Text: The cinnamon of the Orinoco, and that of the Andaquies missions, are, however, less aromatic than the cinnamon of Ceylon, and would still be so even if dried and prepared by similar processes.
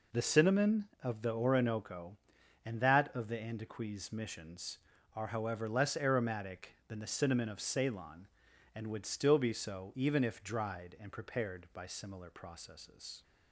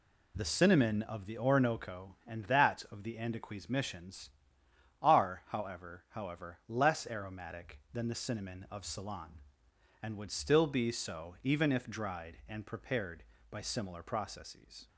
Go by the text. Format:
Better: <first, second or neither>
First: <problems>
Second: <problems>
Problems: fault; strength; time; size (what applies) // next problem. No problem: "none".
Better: first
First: none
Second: says "however" twice; at 6.0 s